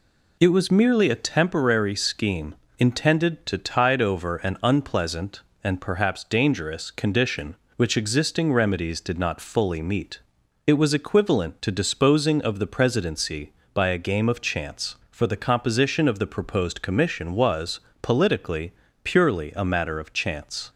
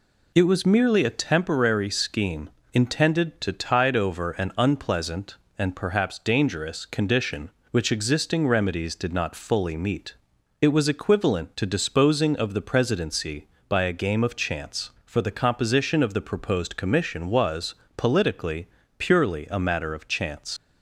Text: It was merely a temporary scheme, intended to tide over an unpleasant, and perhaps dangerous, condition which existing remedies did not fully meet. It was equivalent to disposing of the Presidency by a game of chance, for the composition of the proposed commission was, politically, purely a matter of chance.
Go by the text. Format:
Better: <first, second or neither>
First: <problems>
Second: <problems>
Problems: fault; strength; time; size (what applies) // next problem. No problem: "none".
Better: first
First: none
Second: leaves "chance" unfinished; at 20.5 s; 75 ms